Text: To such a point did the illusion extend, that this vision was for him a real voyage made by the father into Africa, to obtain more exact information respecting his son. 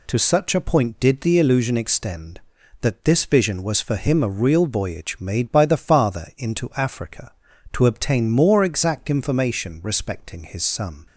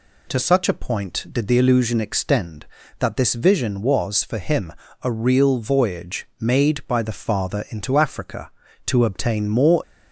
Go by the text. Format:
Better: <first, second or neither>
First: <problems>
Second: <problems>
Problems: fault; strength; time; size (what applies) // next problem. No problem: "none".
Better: first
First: none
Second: pauses between "him" and "a"; slight; at 4.7 s; 0.28 s long // stops before "exact information respecting his son"; at 9.8 s